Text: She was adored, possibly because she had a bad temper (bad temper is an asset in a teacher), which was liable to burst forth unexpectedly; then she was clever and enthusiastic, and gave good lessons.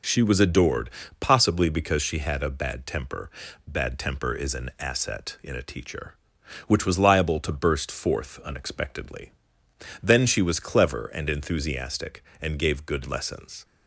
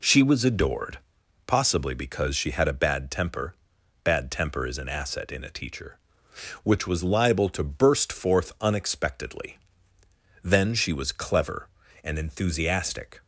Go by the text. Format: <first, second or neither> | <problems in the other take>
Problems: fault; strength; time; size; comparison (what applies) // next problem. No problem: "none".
first | stops before "and gave good lessons"; at 13.2 s